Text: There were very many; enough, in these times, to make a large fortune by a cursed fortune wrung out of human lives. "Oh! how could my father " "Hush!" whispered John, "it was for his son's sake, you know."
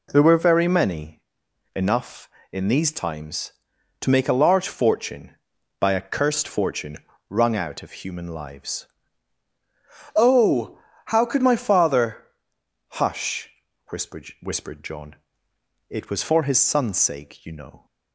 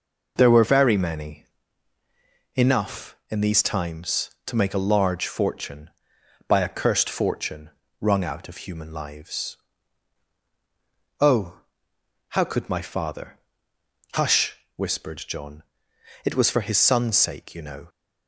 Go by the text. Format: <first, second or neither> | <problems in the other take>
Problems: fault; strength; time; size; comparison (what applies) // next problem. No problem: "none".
second | pauses between "fortune" and "wrung"; slight; at 6.9 s; 0.32 s long; slight in the second // says "whispered" twice; at 14.4 s